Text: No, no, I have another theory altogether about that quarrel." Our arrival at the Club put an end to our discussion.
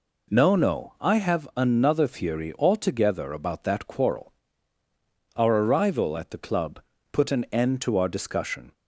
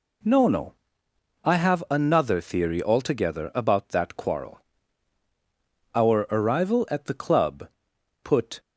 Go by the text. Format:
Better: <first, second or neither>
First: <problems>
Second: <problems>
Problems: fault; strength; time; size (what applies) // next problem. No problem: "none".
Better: first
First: pauses between "Club" and "put"; slight; at 6.8 s; 0.30 s long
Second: pauses between "Club" and "put"; noticeable; at 7.6 s; 0.52 s long // stops before "an end to our discussion"; at 8.5 s